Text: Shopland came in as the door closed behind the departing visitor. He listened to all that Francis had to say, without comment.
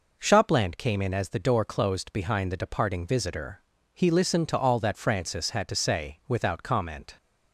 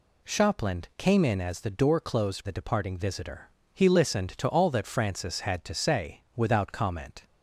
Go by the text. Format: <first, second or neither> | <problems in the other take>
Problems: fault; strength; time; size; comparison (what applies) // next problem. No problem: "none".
first | skips "behind"; at 2.4 s